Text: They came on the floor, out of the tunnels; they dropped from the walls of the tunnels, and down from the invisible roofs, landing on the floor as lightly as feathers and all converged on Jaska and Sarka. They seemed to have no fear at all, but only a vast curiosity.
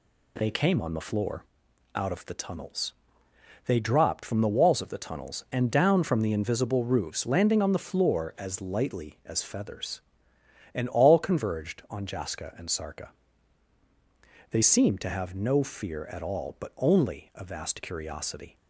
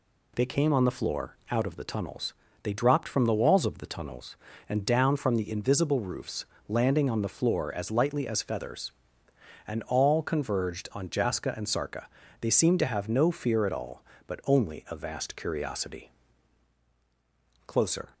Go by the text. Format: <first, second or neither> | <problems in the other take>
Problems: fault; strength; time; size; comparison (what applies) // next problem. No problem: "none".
first | goes on to say "Closer"; slight; from 17.6 s on; 0.48 s long